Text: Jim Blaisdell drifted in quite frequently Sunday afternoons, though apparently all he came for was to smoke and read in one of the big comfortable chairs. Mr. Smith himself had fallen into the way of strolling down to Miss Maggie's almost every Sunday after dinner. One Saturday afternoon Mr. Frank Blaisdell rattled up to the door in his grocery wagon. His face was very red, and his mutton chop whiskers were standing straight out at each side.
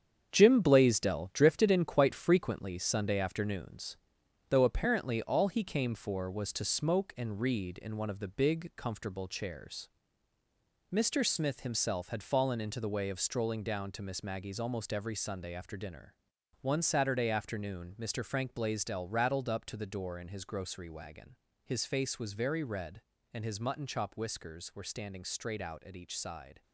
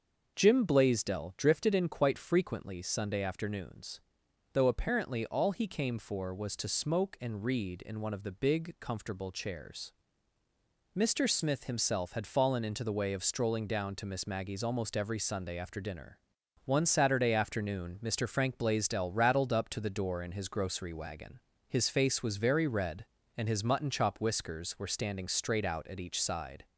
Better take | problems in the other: second | gets quieter; strong; throughout; 8 dB // starts louder than the rest; strong; until 1.3 s; 8 dB; also in the second

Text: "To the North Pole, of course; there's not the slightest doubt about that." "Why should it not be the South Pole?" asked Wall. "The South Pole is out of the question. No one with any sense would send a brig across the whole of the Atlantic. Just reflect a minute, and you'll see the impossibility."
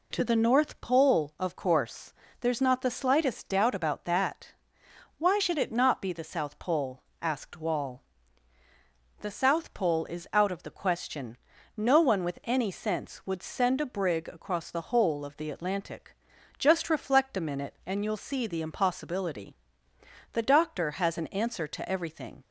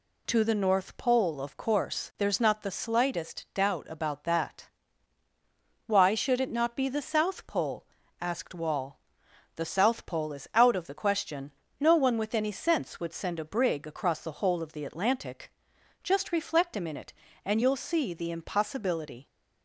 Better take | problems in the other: second | goes on to say "The doctor has an answer to everything"; strong; from 20.3 s on; 2.1 s long

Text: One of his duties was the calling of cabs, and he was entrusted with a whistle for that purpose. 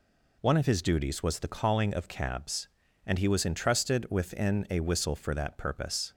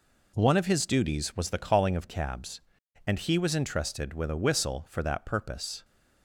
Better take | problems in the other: second | says "within" for "with"; at 4.0 s

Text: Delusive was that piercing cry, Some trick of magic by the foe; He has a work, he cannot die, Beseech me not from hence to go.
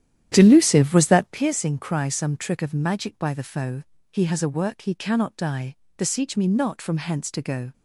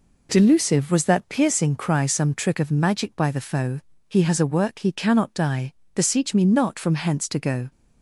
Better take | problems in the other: second | starts louder than the rest; strong; until 1.4 s; 11 dB

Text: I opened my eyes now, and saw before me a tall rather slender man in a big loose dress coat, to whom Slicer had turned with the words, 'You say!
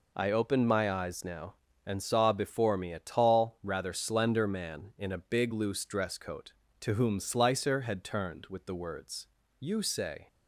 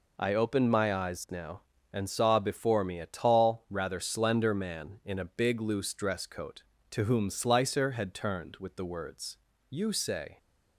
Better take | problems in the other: neither | none

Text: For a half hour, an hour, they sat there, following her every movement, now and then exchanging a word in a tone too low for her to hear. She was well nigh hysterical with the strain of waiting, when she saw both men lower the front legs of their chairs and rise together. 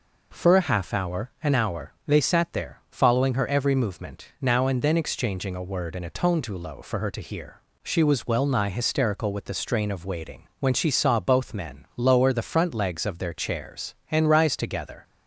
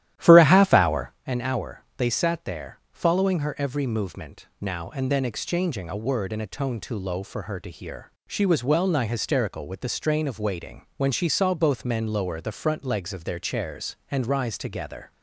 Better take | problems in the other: first | starts louder than the rest; strong; until 1.2 s; 12.5 dB

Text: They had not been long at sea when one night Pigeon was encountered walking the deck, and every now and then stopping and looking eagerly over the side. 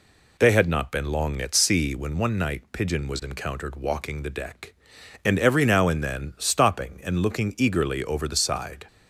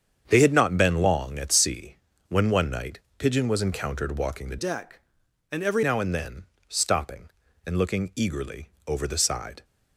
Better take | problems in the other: first | starts louder than the rest; strong; until 1.2 s; 7.5 dB // pauses between "sea" and "when"; slight; at 1.9 s; 0.34 s long // pauses between "night" and "Pigeon"; slight; at 2.9 s; 0.20 s long // changes voice from "deck" to "every"; from 4.5 to 5.8 s; 1.3 s long // pauses between "then" and "stopping"; slight; at 6.4 s; 0.24 s long // pauses between "eagerly" and "over"; slight; at 8.6 s; 0.16 s long

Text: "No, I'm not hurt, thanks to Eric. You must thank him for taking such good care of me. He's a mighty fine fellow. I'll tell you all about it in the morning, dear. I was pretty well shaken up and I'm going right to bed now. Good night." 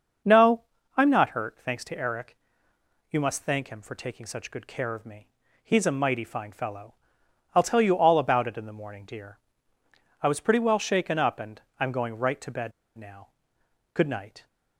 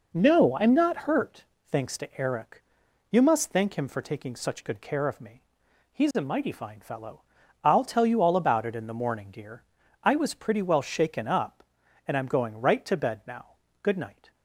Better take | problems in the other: second | starts louder than the rest; until 1.5 s; 6 dB // pauses between "and" and "I'm"; slight; at 11.6 s; 0.18 s long // pauses between "bed" and "now"; slight; at 12.7 s; 0.25 s long

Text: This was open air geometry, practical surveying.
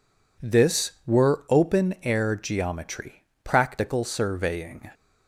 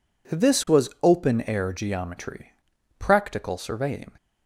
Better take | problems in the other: second | says "were" for "was"; at 1.0 s

